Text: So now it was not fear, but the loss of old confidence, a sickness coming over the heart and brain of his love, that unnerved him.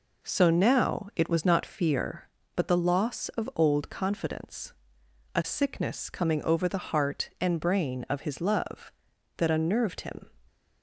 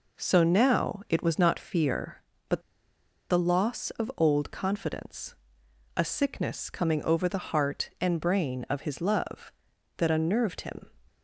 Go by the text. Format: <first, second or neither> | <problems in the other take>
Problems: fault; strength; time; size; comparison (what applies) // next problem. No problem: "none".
first | pauses between "but" and "the"; noticeable; at 2.6 s; 0.68 s long